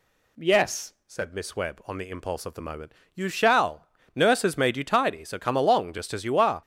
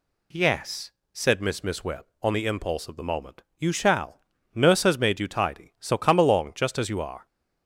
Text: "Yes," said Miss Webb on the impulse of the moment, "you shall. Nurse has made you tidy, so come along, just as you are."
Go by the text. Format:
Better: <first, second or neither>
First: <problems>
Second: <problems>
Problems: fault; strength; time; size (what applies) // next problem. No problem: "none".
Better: first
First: none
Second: says "Miss" twice; at 1.6 s